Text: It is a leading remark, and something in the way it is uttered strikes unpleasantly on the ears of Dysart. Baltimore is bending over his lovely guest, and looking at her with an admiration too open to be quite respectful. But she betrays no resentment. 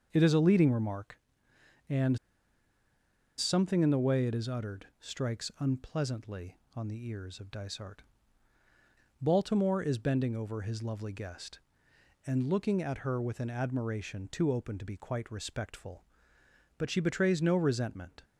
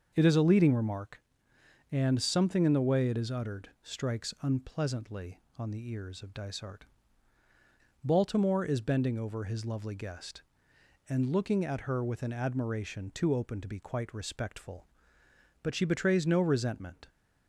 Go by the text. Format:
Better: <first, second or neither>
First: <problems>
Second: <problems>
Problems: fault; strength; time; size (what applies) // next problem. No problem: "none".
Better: second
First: starts louder than the rest; until 1.1 s; 6.5 dB // pauses between "and" and "something"; at 2.1 s; 1.1 s long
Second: starts louder than the rest; until 1.1 s; 6.5 dB